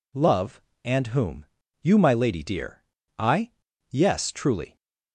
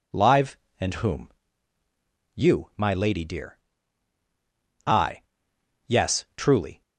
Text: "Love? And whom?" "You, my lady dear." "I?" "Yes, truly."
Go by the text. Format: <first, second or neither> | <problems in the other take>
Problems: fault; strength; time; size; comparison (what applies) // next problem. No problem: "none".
first | says "Live" for "Love"; at 0.1 s